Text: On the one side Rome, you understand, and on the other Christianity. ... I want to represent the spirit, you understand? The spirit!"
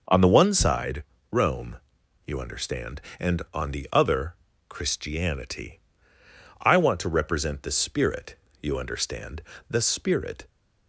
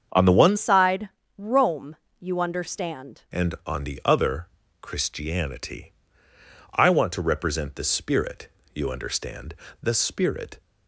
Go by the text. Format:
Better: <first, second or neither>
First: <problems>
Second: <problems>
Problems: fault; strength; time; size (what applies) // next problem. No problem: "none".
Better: first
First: pauses between "side" and "Rome"; slight; at 1.0 s; 0.28 s long // pauses between "other" and "Christianity"; slight; at 4.3 s; 0.34 s long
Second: starts louder than the rest; strong; until 1.4 s; 7 dB // changes voice from "side" to "understand"; from 0.5 to 3.2 s; 2.7 s long // pauses between "side" and "Rome"; slight; at 1.0 s; 0.28 s long // pauses between "other" and "Christianity"; slight; at 4.4 s; 0.34 s long